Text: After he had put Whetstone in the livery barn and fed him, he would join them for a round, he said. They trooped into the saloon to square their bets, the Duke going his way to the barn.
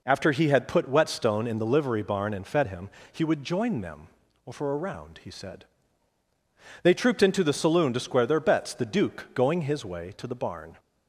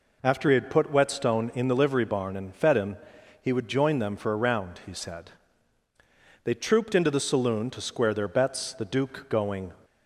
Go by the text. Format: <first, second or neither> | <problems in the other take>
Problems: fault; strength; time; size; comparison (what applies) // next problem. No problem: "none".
first | stops before "his way to the barn"; at 9.8 s